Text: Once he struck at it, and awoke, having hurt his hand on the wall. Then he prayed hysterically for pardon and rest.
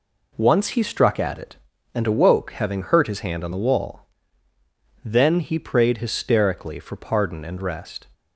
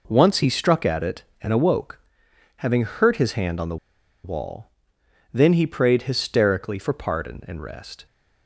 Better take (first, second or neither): first